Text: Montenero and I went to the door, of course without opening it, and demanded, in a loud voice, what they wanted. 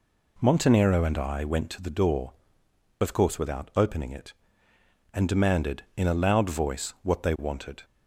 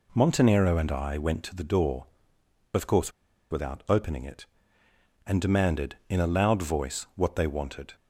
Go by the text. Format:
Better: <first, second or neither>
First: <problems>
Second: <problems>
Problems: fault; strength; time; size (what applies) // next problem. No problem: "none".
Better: first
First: none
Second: pauses between "course" and "without"; at 3.1 s; 0.40 s long